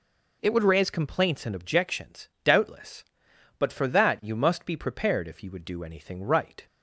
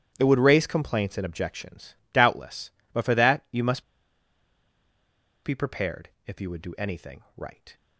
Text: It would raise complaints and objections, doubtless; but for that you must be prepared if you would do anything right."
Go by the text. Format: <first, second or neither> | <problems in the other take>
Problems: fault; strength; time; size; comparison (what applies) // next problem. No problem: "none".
first | starts louder than the rest; strong; until 1.1 s; 10.5 dB // pauses between "must" and "be"; strong; at 3.8 s; 1.6 s long // pauses between "prepared" and "if"; slight; at 6.0 s; 0.16 s long